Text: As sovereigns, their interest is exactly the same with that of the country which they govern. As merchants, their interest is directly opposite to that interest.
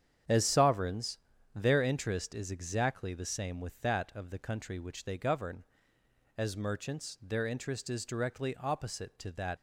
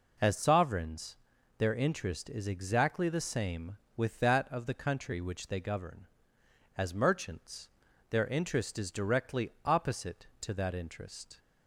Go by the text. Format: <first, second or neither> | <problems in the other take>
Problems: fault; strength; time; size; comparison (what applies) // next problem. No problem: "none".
second | starts louder than the rest; strong; until 1.6 s; 8.5 dB // stops before "interest"; at 9.5 s